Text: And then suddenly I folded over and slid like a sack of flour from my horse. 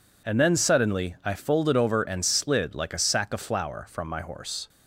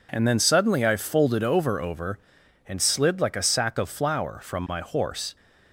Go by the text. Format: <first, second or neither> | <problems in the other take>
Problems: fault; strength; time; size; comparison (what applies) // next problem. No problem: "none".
first | says "over" twice; at 1.7 s